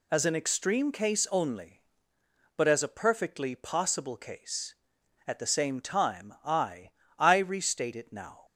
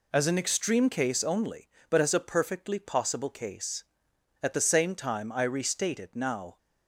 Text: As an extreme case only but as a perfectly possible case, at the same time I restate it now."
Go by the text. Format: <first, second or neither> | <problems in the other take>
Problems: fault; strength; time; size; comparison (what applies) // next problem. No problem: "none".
second | says "I" twice; at 7.1 s